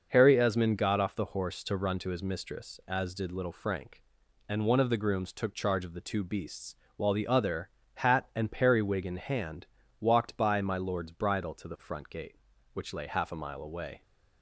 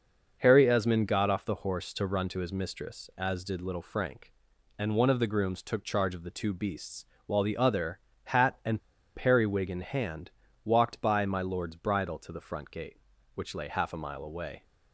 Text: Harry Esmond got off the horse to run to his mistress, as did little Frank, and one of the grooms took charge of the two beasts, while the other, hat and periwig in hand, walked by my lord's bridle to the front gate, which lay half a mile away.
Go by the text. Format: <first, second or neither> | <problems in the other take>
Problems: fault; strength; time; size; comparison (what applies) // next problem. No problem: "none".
first | starts louder than the rest; noticeable; until 1.4 s; 6 dB; noticeable in the first // pauses between "and" and "periwig"; at 8.7 s; 0.36 s long